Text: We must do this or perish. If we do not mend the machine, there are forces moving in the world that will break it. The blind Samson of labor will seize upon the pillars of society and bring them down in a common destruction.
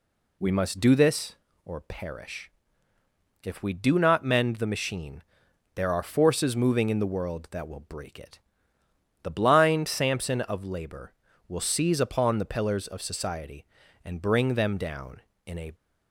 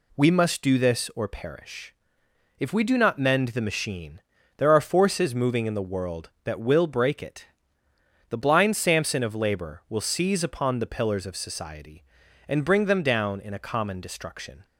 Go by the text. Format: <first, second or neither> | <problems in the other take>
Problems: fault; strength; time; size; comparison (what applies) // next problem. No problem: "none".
second | stops before "common destruction"; at 15.7 s